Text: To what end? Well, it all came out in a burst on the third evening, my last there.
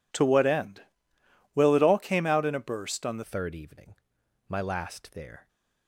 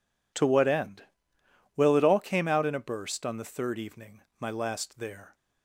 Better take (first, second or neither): second